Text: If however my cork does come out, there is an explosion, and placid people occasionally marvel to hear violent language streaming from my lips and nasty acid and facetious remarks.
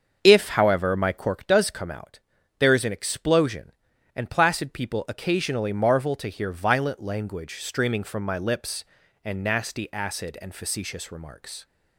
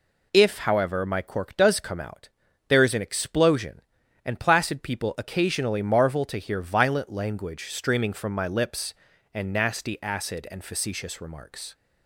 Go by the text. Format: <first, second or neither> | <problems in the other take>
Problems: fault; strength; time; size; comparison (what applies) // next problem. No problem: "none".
second | starts louder than the rest; until 1.4 s; 7 dB